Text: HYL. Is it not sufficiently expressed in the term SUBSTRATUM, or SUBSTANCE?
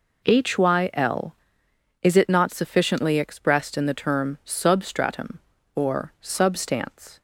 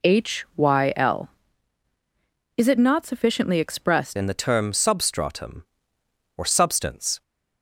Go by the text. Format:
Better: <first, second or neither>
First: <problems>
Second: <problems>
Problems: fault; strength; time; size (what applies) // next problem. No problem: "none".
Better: first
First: none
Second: changes voice at "in"; from 4.1 s on; 3.1 s long